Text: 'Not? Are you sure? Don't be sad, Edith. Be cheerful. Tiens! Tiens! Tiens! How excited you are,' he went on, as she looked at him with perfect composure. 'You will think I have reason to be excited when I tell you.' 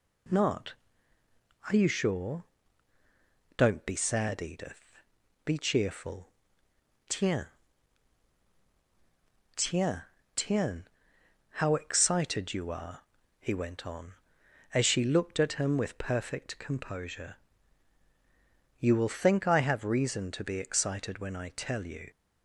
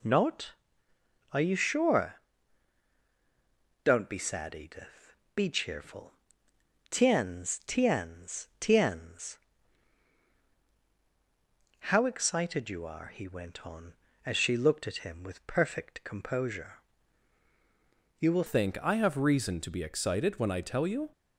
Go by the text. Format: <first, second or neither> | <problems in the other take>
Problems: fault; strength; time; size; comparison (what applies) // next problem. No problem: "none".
first | changes voice at "think"; from 18.4 s on; 2.6 s long